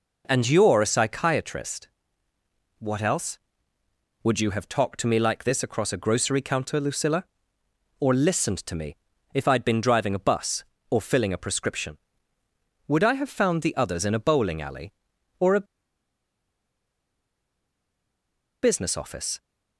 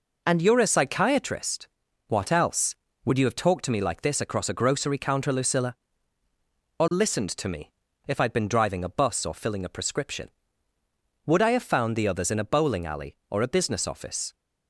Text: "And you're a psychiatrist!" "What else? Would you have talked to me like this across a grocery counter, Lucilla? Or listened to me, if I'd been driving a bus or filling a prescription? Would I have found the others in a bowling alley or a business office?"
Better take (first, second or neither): second